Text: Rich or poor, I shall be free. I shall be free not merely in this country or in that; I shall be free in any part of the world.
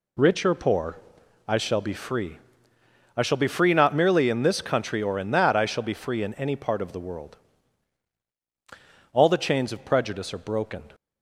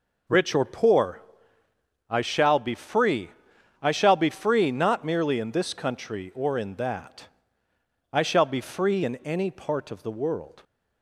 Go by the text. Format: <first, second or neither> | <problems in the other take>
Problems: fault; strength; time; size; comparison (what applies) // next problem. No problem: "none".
second | goes on to say "All the chains of prejudice are broken"; strong; from 9.1 s on; 1.7 s long